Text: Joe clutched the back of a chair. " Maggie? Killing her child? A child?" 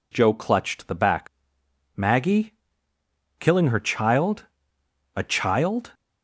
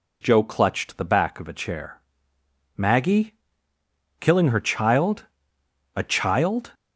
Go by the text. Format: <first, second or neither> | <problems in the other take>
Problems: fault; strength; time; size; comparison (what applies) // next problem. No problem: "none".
second | skips "of a chair"; at 1.4 s